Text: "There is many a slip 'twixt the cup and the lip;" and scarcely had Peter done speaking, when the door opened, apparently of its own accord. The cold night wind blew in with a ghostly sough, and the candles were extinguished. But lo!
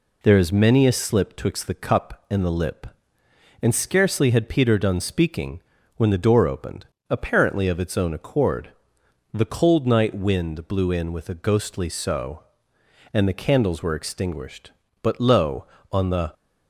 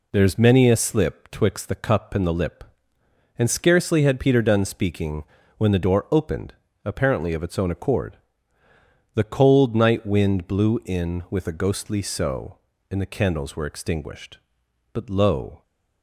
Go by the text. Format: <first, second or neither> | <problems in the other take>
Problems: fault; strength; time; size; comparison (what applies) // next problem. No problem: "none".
second | goes on to say "on the"; slight; from 15.8 s on; 0.44 s long